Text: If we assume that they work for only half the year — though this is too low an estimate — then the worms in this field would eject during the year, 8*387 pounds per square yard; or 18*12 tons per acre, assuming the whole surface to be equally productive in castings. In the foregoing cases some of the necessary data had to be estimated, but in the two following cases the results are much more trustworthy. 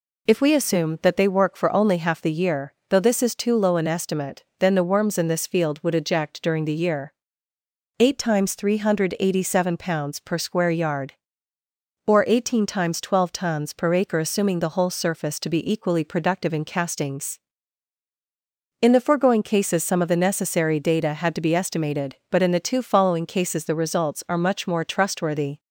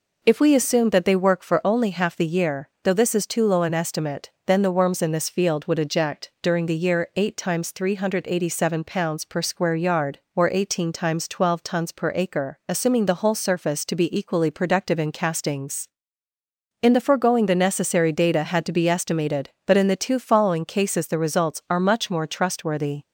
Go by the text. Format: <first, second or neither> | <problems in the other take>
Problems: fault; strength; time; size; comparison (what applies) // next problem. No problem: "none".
first | skips "cases some of"; at 17.4 s